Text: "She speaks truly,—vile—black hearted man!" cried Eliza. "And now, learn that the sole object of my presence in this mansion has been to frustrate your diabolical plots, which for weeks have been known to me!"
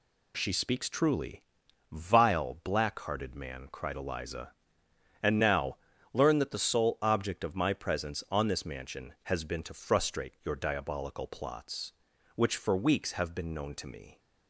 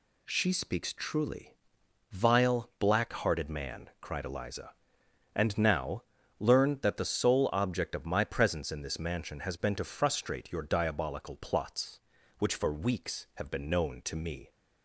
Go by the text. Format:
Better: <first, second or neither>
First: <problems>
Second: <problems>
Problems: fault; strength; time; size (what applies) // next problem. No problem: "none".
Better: second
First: says "on" for "in"; at 8.3 s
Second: none